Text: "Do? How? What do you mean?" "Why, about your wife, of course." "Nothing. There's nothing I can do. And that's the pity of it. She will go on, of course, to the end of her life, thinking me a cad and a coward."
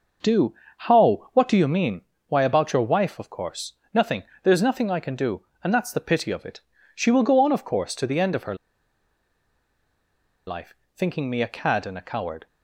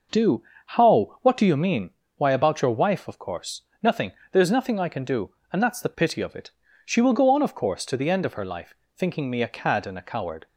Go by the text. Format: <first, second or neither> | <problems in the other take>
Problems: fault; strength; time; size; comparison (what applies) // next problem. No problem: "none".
second | pauses between "her" and "life"; strong; at 8.5 s; 1.9 s long